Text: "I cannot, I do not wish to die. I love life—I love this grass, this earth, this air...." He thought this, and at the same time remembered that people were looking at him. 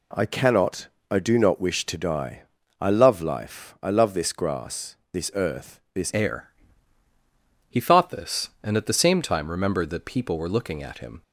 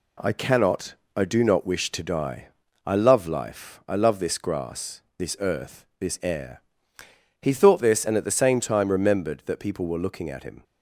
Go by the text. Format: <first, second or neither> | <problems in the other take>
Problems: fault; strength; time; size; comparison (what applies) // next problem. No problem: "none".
second | changes voice at "air"; from 6.1 s on; 5.1 s long